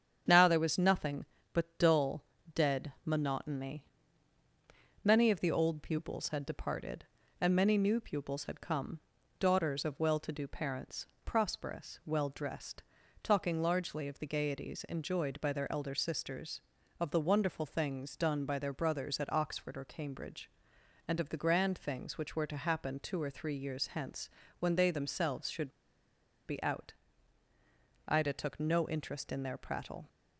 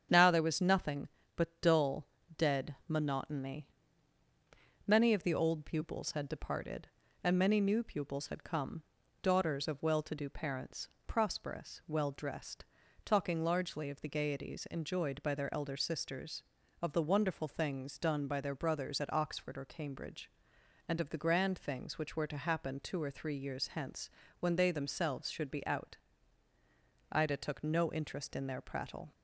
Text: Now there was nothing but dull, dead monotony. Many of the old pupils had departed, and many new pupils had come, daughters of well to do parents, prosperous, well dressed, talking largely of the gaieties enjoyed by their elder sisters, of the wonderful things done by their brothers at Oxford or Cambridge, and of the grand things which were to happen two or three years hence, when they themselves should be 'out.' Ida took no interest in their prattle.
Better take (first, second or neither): second